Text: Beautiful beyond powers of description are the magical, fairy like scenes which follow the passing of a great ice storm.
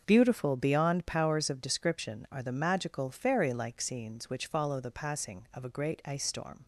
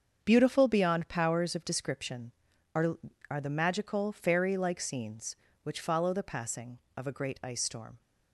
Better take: first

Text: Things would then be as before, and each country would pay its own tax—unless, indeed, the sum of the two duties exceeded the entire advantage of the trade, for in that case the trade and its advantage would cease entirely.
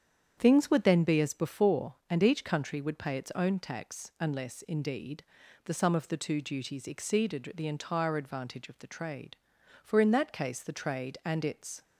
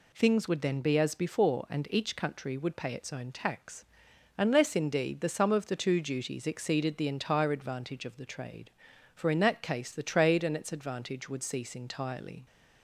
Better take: second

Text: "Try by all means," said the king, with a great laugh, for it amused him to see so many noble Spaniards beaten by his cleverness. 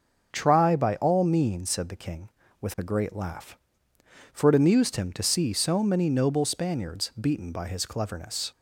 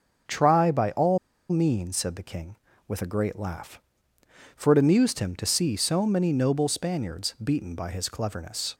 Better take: first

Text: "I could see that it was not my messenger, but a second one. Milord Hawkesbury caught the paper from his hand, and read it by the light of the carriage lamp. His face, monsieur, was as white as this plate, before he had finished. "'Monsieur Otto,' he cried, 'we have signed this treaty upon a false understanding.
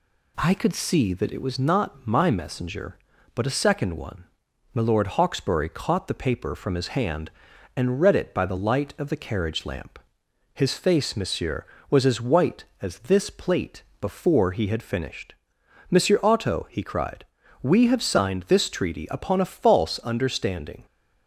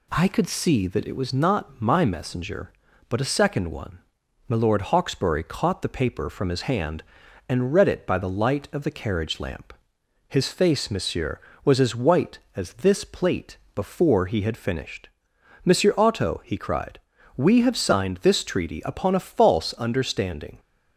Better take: neither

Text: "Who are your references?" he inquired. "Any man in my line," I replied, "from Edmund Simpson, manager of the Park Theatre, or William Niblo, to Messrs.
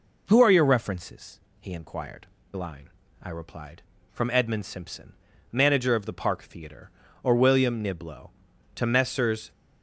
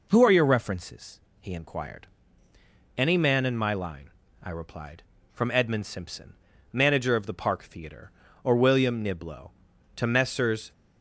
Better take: second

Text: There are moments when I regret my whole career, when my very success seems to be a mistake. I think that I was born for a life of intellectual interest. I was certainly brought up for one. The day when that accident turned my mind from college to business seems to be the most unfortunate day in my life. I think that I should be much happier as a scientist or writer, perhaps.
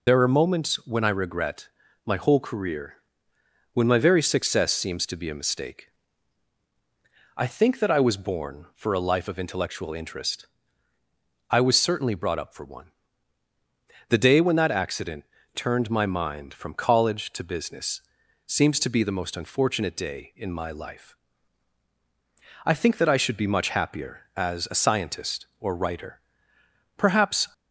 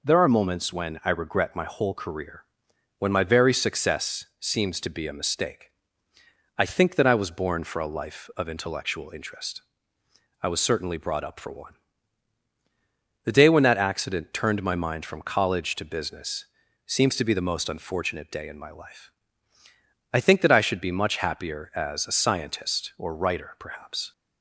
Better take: second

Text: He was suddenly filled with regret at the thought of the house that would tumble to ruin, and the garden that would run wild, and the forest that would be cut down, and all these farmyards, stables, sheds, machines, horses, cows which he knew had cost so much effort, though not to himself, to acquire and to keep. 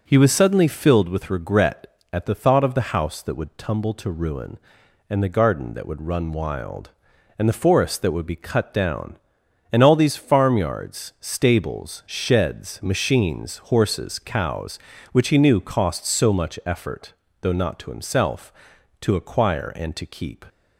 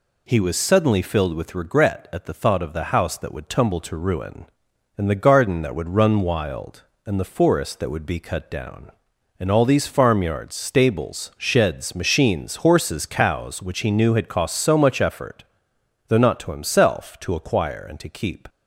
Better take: second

